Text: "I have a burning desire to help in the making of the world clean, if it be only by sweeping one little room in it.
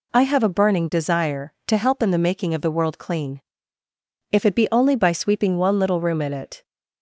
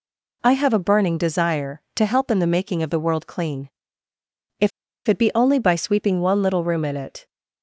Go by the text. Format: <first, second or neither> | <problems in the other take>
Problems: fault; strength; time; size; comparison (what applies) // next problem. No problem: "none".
first | pauses between "if" and "it"; at 4.7 s; 0.37 s long